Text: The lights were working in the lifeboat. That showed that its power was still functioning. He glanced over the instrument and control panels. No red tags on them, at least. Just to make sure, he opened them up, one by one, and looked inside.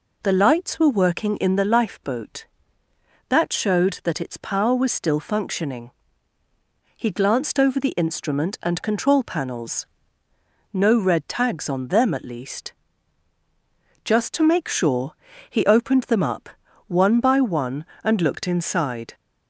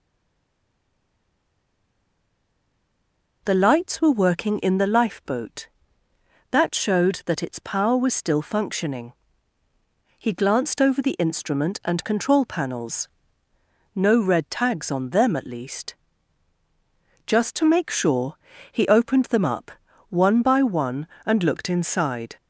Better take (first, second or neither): first